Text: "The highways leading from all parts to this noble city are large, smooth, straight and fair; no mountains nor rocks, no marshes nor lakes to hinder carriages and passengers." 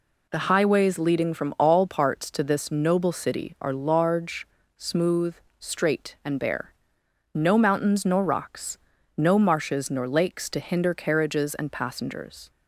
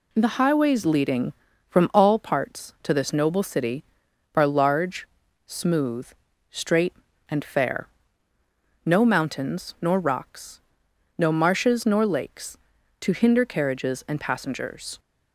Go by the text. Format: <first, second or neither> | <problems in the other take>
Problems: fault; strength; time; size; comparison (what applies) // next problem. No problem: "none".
second | says "bare" for "fair"; at 6.3 s